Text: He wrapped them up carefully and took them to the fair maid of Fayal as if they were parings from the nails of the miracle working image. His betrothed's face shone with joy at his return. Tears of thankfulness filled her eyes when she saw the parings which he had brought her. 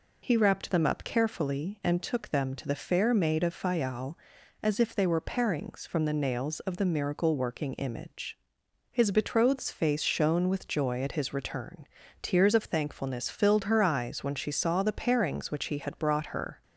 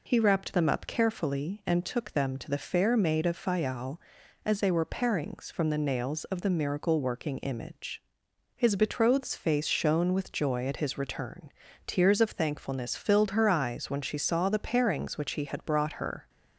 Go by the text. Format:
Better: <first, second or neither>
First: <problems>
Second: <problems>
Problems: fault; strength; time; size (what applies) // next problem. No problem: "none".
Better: first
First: none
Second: skips "if"; at 4.6 s